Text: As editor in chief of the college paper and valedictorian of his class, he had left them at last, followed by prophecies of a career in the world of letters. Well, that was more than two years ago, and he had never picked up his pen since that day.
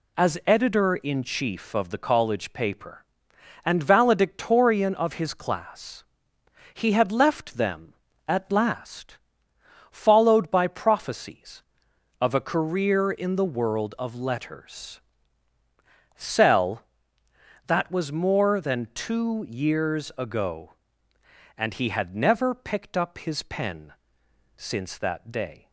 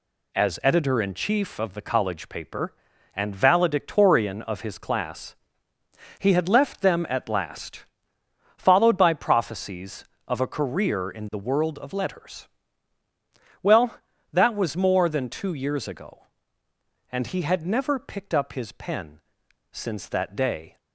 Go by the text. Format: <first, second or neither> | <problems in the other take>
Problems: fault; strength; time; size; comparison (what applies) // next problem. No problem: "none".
second | says "Cell" for "Well"; at 16.1 s // pauses between "pen" and "since"; noticeable; at 23.9 s; 0.64 s long; noticeable in the second